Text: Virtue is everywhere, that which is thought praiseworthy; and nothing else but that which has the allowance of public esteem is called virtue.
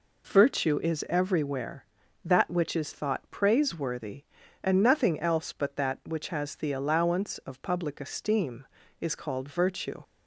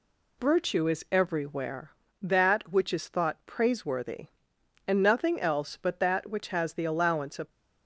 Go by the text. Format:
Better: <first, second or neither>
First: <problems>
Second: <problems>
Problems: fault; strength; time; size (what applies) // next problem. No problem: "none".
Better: first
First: none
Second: stops before "public esteem is called virtue"; at 7.5 s